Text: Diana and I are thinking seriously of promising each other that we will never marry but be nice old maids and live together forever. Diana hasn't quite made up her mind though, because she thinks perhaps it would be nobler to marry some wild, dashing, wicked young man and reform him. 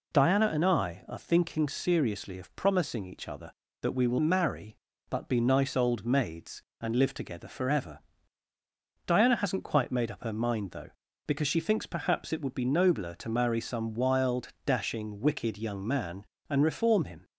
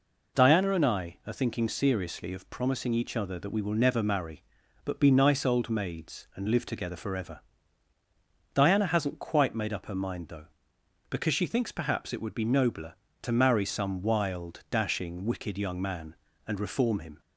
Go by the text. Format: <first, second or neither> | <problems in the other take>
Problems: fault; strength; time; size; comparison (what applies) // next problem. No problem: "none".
second | skips "never"; at 4.1 s